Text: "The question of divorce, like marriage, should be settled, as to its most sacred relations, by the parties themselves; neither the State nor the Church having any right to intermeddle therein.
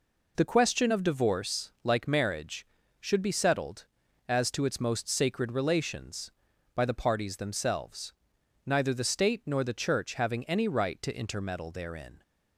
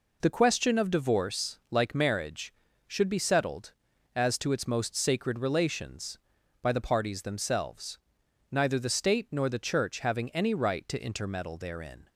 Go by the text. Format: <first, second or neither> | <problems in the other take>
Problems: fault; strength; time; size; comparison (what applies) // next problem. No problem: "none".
neither | none